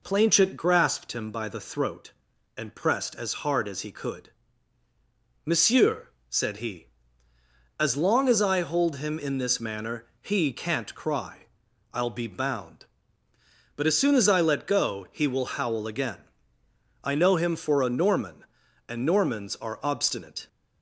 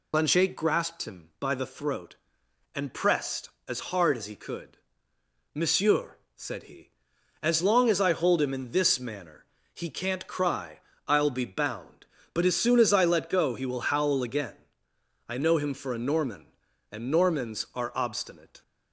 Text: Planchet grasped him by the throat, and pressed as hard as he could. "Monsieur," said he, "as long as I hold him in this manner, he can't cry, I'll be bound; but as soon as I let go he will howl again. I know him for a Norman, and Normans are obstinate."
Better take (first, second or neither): first